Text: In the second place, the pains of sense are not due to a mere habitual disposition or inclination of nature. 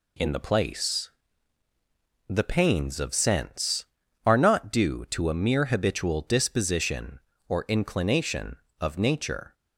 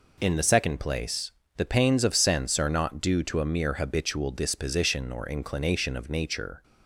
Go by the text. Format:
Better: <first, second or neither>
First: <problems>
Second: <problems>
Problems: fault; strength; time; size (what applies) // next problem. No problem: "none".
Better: second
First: skips "second"; at 0.3 s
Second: none